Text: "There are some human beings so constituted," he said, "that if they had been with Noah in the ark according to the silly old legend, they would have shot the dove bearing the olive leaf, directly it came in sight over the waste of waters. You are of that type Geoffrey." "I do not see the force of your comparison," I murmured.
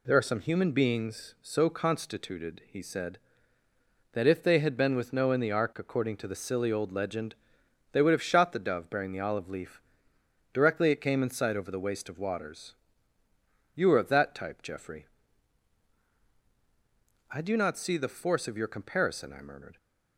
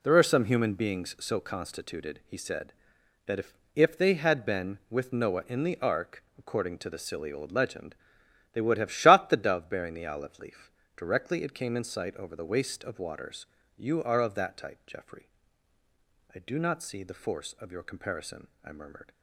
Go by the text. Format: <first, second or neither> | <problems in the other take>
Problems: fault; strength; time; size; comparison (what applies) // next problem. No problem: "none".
first | says "if" twice; at 3.7 s